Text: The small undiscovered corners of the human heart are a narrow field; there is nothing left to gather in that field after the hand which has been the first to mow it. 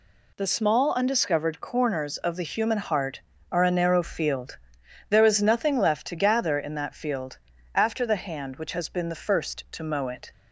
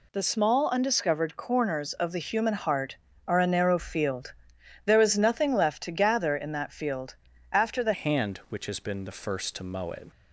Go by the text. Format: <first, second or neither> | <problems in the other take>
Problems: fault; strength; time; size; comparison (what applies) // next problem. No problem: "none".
first | pauses between "field" and "after"; at 7.1 s; 0.38 s long; also in the first // changes voice at "hand"; from 7.9 s on; 2.2 s long